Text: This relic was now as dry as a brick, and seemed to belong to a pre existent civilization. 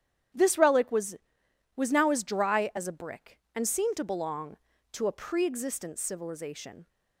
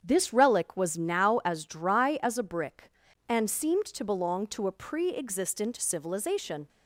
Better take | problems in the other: second | starts louder than the rest; strong; until 1.9 s; 9.5 dB; strong in the second // says "was" twice; at 1.7 s

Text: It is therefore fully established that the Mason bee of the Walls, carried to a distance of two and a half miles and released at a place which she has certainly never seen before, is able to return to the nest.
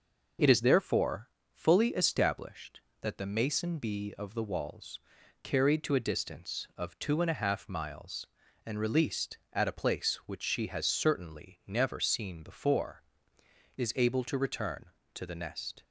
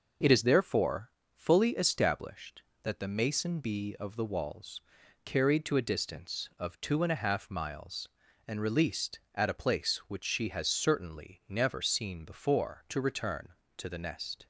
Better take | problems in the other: first | pauses between "therefore" and "fully"; slight; at 1.0 s; 0.24 s long; slight in the first // skips "is able"; at 12.8 s

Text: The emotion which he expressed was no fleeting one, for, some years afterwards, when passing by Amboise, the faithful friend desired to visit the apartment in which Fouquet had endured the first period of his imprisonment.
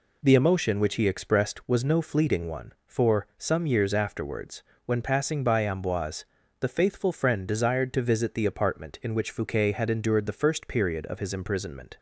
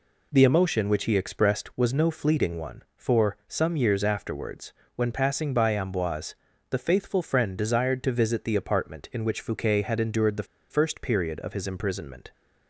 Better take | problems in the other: first | pauses between "the" and "first"; slight; at 10.4 s; 0.26 s long

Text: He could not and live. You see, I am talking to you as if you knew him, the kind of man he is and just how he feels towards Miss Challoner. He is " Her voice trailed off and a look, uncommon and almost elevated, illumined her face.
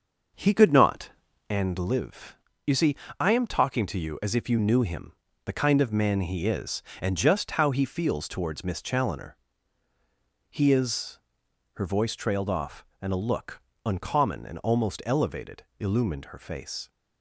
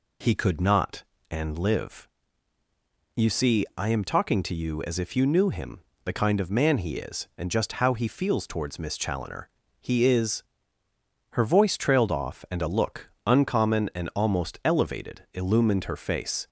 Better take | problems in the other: second | starts louder than the rest; until 1.6 s; 6 dB

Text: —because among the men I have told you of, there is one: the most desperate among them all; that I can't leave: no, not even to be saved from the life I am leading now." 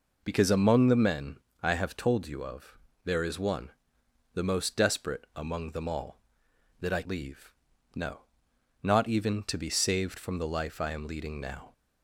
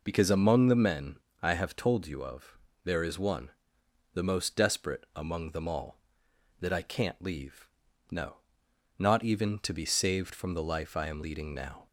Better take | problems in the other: second | pauses between "men" and "I"; slight; at 1.3 s; 0.24 s long; slight in the second // skips "can't"; at 7.0 s

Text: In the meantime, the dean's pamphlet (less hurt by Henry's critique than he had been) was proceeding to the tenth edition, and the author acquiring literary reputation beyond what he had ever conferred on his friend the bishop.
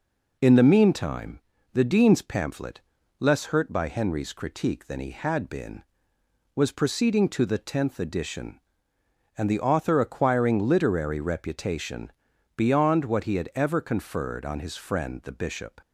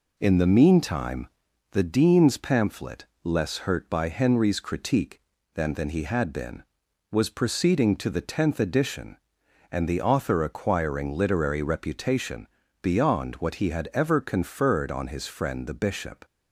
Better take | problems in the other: first | says "than" twice; at 5.7 s // pauses between "reputation" and "beyond"; slight; at 12.4 s; 0.34 s long; also in the first

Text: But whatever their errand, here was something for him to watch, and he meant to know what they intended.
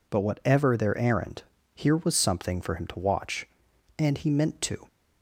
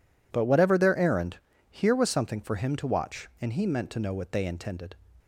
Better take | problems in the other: second | stops before "know what they intended"; at 4.8 s

